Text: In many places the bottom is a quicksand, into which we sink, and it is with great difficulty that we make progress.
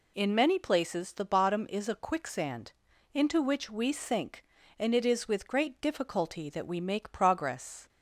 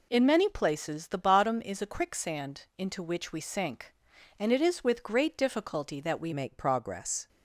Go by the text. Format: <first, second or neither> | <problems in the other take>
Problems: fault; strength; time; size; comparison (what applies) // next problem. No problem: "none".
first | changes voice at "make"; from 6.3 s on; 0.9 s long